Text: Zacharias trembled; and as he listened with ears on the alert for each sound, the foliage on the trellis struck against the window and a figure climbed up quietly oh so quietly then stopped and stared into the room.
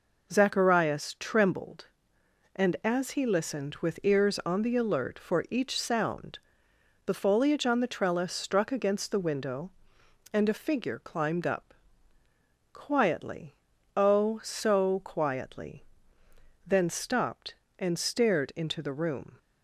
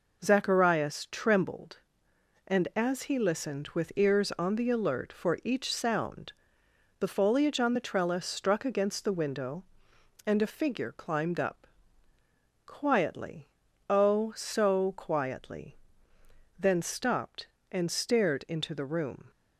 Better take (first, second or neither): neither